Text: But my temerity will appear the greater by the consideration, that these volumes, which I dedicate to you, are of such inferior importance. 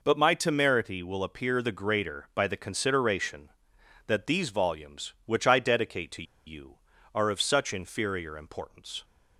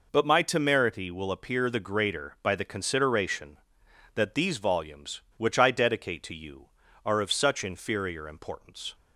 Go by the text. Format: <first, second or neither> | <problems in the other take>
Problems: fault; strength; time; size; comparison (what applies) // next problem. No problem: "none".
second | pauses between "to" and "you"; slight; at 6.2 s; 0.23 s long